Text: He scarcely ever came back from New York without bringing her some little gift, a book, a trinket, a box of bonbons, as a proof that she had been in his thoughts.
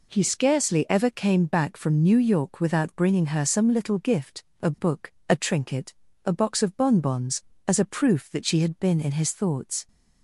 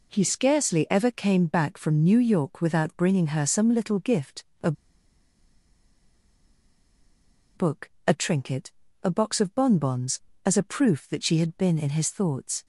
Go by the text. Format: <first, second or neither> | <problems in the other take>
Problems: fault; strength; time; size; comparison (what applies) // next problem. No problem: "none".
first | pauses between "a" and "book"; strong; at 4.7 s; 2.8 s long